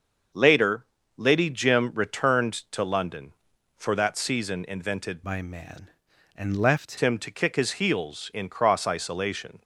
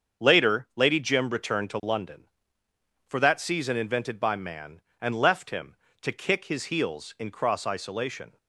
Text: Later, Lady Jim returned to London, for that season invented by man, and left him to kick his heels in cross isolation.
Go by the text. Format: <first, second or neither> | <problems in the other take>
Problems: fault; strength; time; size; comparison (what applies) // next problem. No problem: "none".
second | starts louder than the rest; until 1.6 s; 6.5 dB; also in the second // changes voice from "by" to "left"; from 5.2 to 6.9 s; 1.7 s long